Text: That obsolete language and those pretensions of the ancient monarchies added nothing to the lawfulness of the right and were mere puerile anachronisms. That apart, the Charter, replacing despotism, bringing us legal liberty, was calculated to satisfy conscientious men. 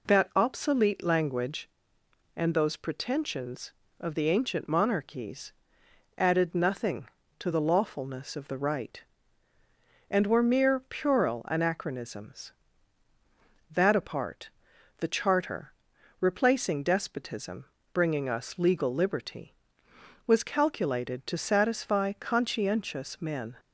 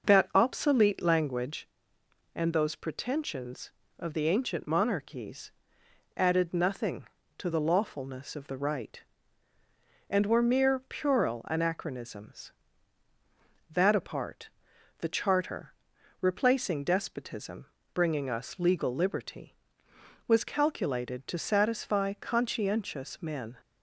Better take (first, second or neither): first